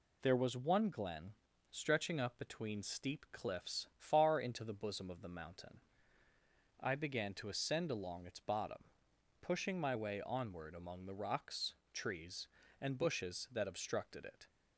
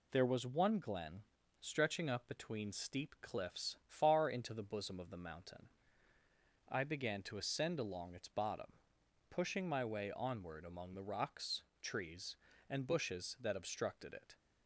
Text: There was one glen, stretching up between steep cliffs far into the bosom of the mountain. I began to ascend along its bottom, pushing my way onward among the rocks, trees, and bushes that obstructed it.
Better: neither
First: none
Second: none

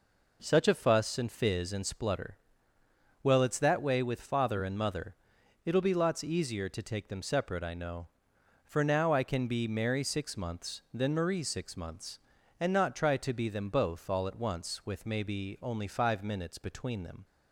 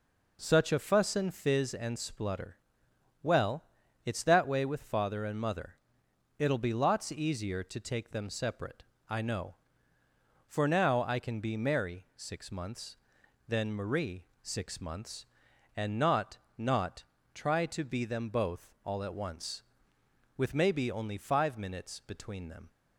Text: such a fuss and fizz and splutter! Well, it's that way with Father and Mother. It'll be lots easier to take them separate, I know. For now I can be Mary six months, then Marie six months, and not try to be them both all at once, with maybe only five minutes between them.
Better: first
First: none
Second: pauses between "Marie" and "six"; slight; at 14.2 s; 0.18 s long // says "not" twice; at 16.5 s

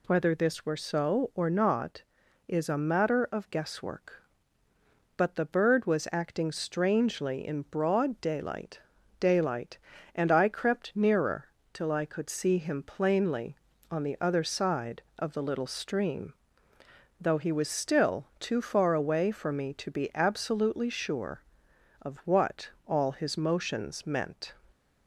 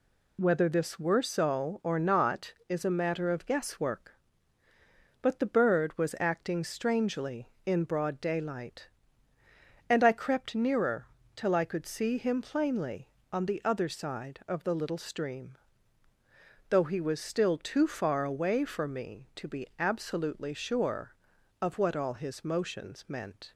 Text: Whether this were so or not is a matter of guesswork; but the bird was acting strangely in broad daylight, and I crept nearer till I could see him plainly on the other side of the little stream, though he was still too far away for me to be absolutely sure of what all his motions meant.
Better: second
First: says "daylight" twice; at 9.1 s // pauses between "nearer" and "till"; slight; at 11.4 s; 0.26 s long // pauses between "what" and "all"; slight; at 22.6 s; 0.16 s long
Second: pauses between "nearer" and "till"; slight; at 11.0 s; 0.28 s long

